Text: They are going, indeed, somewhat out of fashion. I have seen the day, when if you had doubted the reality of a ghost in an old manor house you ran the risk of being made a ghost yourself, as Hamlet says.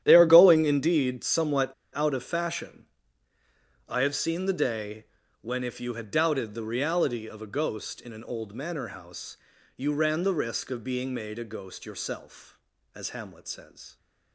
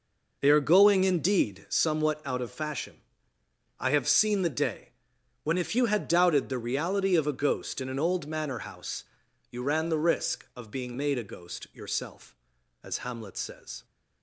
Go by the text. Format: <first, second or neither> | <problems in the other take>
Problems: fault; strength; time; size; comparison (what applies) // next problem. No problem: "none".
second | starts louder than the rest; strong; until 1.0 s; 10.5 dB // pauses between "somewhat" and "out"; slight; at 1.7 s; 0.22 s long // pauses between "house" and "you"; at 9.3 s; 0.38 s long; noticeable in the second